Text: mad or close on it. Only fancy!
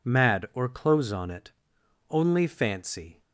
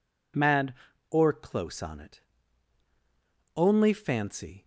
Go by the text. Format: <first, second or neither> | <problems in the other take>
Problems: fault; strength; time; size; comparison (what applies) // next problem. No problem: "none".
neither | none